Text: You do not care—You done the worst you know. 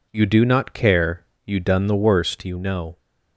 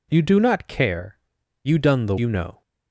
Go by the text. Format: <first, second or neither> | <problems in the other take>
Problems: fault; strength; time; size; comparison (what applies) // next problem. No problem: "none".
first | skips "worst"; at 2.1 s